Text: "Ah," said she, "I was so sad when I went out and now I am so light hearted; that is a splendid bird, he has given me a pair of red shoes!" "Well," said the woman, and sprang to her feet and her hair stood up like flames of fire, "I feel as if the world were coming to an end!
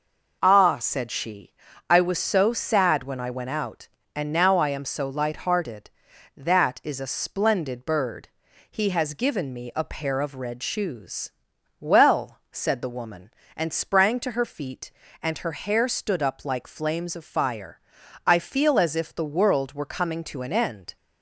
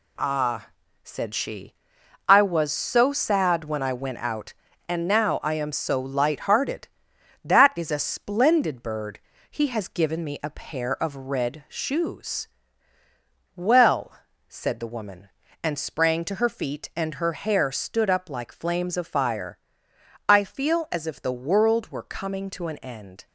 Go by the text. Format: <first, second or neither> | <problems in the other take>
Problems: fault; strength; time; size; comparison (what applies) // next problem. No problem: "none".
first | gets quieter; throughout; 7 dB